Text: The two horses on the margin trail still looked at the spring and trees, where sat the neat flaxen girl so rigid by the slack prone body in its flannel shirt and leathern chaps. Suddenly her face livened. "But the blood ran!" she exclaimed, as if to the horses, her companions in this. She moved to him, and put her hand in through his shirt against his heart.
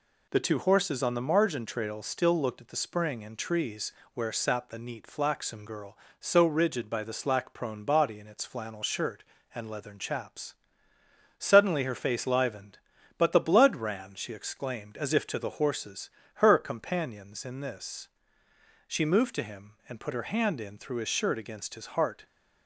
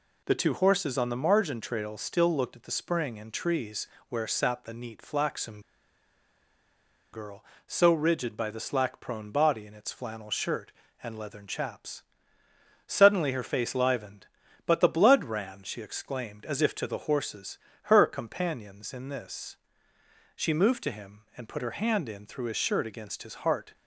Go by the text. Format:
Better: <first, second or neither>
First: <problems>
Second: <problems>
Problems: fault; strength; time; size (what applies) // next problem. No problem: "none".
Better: first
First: none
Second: pauses between "flaxen" and "girl"; strong; at 5.6 s; 1.5 s long